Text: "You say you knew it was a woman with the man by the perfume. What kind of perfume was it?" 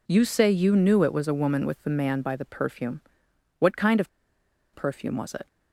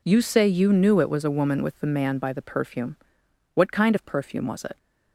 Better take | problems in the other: second | pauses between "of" and "perfume"; noticeable; at 4.0 s; 0.65 s long

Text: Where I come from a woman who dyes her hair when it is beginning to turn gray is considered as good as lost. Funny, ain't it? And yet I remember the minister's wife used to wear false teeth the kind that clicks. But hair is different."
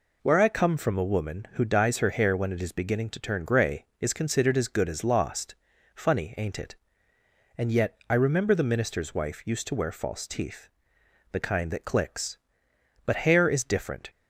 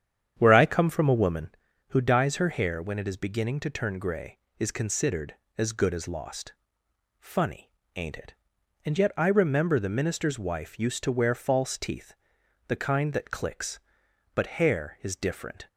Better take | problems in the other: first | starts louder than the rest; strong; until 1.6 s; 8.5 dB // pauses between "teeth" and "the"; noticeable; at 12.1 s; 0.54 s long; noticeable in the first

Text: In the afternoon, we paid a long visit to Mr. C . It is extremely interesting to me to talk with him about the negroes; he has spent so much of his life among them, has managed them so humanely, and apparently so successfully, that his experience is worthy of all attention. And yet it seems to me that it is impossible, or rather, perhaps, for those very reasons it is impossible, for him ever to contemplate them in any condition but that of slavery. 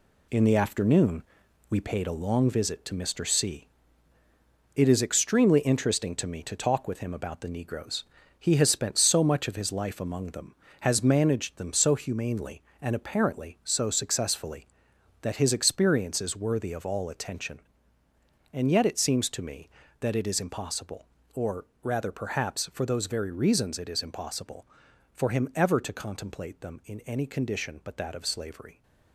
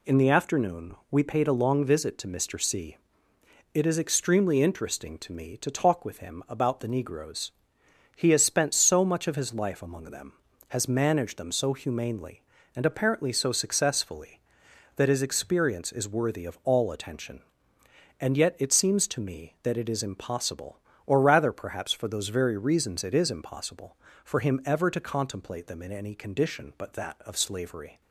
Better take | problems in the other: second | gets quieter; strong; throughout; 7.5 dB // pauses between "or" and "rather"; slight; at 21.6 s; 0.18 s long

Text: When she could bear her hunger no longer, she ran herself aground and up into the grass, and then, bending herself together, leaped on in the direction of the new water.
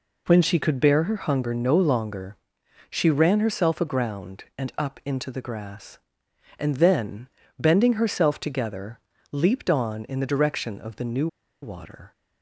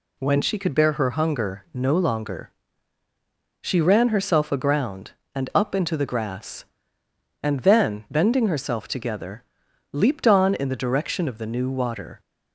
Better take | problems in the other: second | pauses between "new" and "water"; slight; at 11.2 s; 0.35 s long

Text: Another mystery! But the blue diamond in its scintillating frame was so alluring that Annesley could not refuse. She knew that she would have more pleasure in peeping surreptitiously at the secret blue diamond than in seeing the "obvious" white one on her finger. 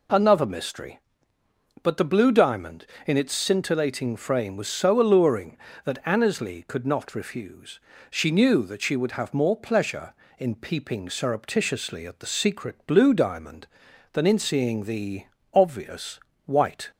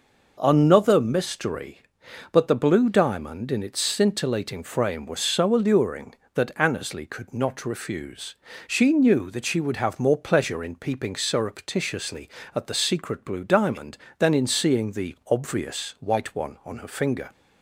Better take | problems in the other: second | pauses between "the" and "obvious"; slight; at 15.2 s; 0.28 s long // pauses between "obvious" and "white"; slight; at 16.1 s; 0.26 s long // stops before "one on her finger"; at 16.9 s

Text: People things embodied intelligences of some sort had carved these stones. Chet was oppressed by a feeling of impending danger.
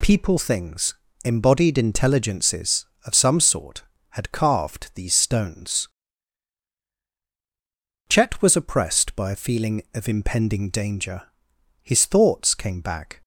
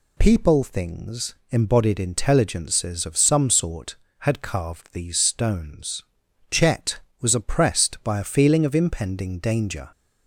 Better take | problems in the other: second | pauses between "things" and "embodied"; slight; at 0.9 s; 0.28 s long; slight in the second // goes on to say "His thoughts came back"; from 11.8 s on; 1.3 s long

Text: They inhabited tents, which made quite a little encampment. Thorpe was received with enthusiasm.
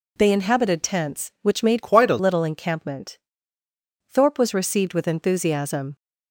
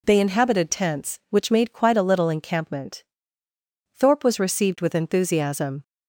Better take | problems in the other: second | changes voice from "quite" to "a"; from 1.8 to 2.1 s; 0.3 s long

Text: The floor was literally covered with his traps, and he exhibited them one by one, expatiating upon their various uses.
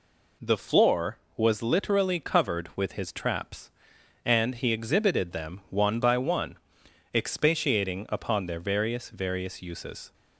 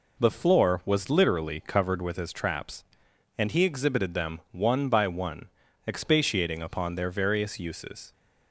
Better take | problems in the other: second | says "various" twice; at 9.0 s

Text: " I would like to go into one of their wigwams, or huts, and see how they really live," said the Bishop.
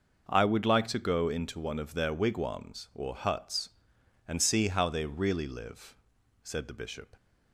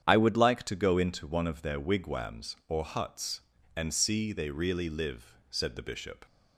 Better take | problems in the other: first | starts louder than the rest; strong; until 1.0 s; 9 dB // skips "how"; at 4.3 s

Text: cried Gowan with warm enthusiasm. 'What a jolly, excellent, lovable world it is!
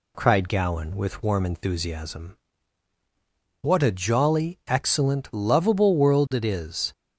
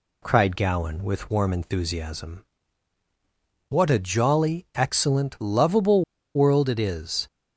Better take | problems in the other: first | pauses between "lovable" and "world"; slight; at 6.0 s; 0.32 s long

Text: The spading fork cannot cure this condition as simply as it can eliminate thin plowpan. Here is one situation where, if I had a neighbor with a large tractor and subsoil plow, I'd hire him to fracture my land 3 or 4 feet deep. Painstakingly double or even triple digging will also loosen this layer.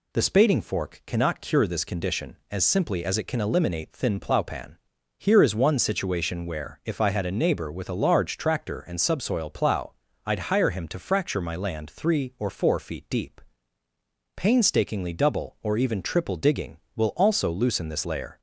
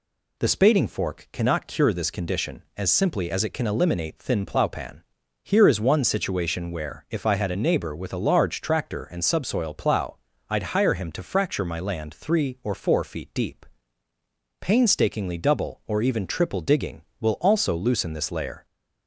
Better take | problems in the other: neither | none

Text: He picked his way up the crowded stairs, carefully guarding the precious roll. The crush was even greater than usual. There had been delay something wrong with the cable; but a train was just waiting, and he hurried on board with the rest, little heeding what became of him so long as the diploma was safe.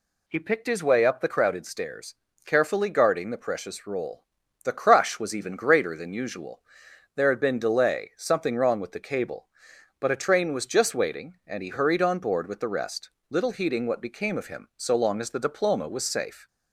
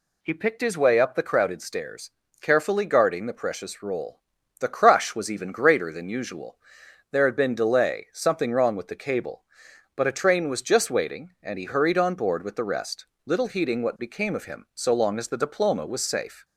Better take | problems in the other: neither | none

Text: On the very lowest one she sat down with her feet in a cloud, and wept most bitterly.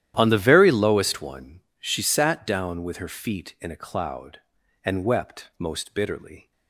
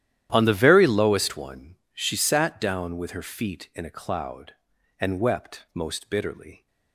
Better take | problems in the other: neither | starts louder than the rest; strong; the same in both // pauses between "one" and "she"; slight; the same in both

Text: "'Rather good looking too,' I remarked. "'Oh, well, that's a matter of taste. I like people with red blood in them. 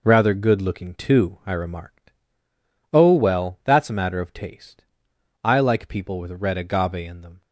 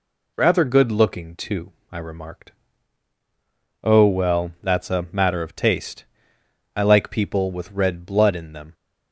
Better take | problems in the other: second | says "agave" for "blood"; at 6.5 s

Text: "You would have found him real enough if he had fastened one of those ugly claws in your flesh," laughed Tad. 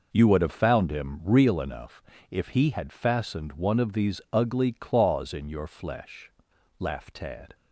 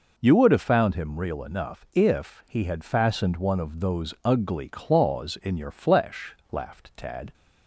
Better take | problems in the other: second | pauses between "enough" and "if"; slight; at 2.0 s; 0.28 s long // says "these" for "those"; at 3.9 s

